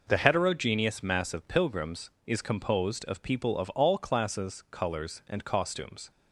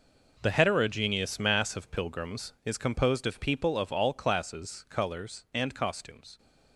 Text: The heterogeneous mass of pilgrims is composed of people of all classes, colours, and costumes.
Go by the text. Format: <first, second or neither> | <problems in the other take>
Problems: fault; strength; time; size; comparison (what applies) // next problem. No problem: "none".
first | gets quieter; strong; throughout; 14 dB